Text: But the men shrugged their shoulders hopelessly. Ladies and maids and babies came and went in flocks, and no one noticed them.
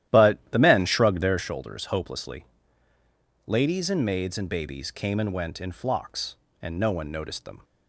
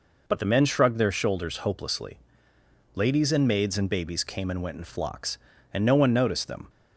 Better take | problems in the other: second | starts louder than the rest; strong; until 1.5 s; 12.5 dB

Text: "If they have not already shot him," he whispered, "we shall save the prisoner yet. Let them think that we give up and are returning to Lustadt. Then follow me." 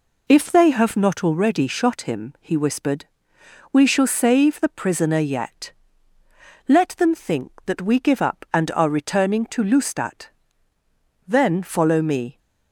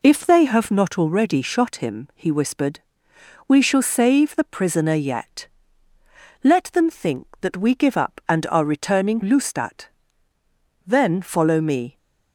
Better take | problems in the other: first | skips "to"; at 9.2 s

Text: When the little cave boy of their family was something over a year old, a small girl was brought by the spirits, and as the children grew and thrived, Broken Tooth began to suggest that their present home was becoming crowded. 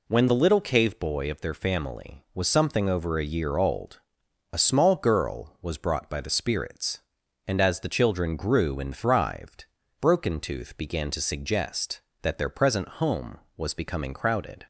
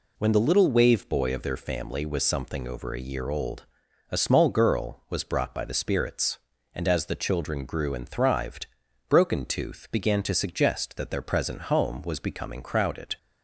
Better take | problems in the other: first | says "wave" for "cave"; at 0.7 s

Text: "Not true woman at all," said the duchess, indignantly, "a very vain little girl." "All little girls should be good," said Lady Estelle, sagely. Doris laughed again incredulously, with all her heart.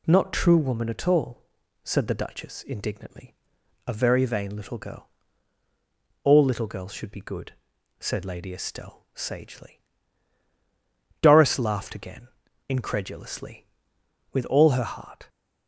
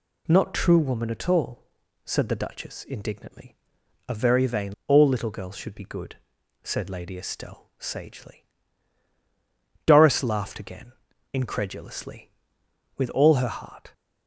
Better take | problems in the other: first | skips "little girl"; at 4.8 s // pauses between "again" and "incredulously"; at 10.9 s; 0.38 s long; also in the first

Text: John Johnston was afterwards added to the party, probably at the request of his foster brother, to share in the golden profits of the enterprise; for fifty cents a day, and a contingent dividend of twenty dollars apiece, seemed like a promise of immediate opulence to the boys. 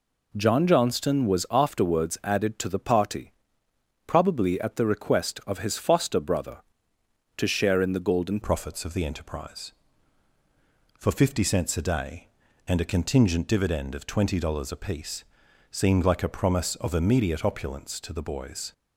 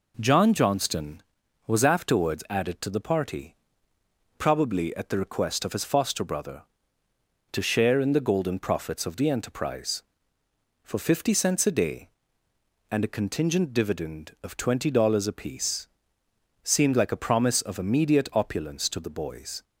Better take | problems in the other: second | changes voice at "profits"; from 8.4 s on; 10.3 s long

